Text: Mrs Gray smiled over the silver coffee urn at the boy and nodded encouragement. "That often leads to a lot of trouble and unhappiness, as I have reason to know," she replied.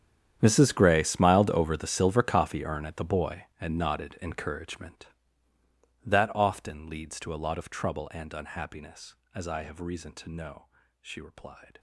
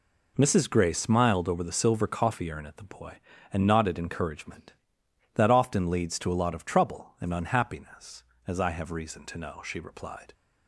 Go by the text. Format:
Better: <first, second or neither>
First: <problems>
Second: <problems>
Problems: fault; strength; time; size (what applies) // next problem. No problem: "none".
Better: second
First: gets quieter; strong; throughout; 18.5 dB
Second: none